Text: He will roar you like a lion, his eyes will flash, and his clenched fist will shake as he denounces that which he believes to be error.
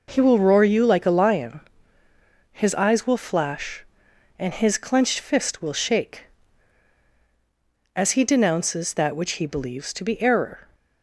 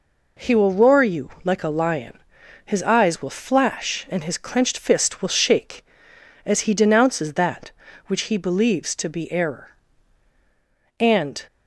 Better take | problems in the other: first | goes on to say "And"; slight; from 11.0 s on; 0.46 s long

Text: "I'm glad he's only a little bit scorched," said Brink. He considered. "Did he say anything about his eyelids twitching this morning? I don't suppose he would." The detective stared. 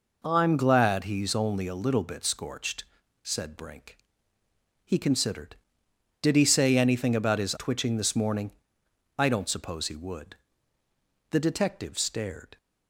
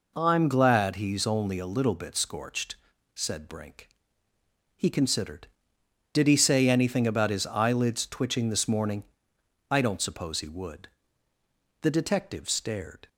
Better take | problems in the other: second | skips "eyelids"; at 7.5 s

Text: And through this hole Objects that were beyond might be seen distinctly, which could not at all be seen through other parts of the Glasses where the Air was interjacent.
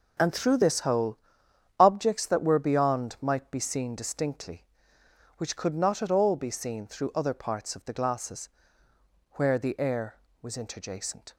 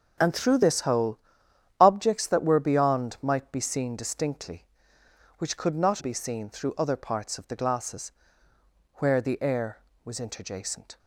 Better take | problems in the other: first | starts louder than the rest; strong; until 1.8 s; 7 dB // pauses between "hole" and "Objects"; noticeable; at 1.1 s; 0.62 s long; noticeable in the first // skips "at all"; at 6.0 s // pauses between "Glasses" and "where"; noticeable; at 8.1 s; 0.84 s long; noticeable in the first

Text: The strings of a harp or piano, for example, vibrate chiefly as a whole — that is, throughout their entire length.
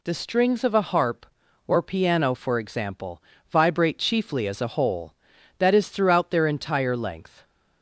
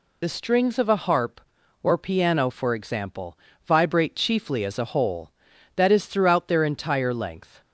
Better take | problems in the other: first | loses the start of "The"; at 0.2 s; 50 ms

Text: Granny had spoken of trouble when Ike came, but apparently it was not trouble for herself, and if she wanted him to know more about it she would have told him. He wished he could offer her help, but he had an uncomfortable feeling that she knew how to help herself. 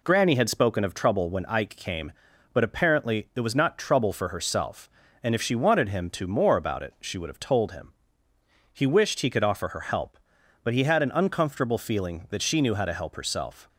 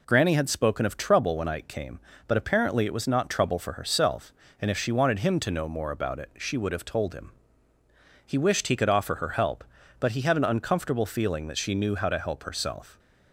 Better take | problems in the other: second | skips "know"; at 6.2 s

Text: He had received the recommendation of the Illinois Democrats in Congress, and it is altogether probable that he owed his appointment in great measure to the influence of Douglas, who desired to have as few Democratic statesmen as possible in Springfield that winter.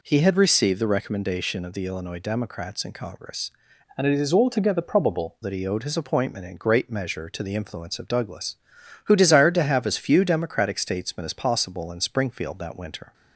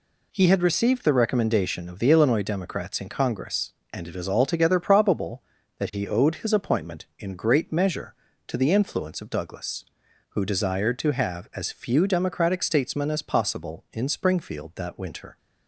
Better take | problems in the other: second | changes voice from "and" to "probable"; from 3.9 to 5.3 s; 1.4 s long

